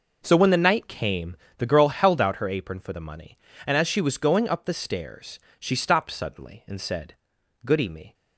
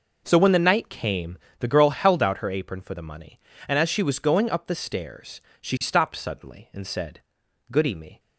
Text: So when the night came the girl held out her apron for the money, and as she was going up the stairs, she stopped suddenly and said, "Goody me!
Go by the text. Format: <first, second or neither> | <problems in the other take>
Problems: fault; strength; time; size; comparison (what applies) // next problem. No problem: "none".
neither | pauses between "came" and "the"; slight; the same in both